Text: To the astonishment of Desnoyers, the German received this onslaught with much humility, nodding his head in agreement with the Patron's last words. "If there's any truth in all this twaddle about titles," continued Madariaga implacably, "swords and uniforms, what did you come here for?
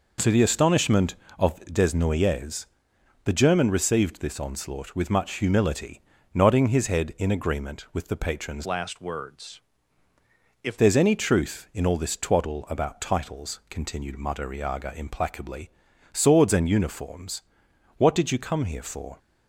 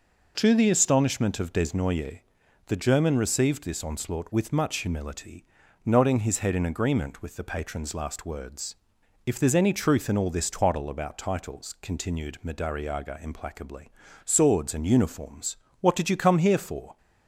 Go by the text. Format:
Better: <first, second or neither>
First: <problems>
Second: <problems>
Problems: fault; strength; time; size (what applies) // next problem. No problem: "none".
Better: second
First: changes voice from "last" to "If"; from 8.6 to 10.7 s; 2.1 s long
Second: none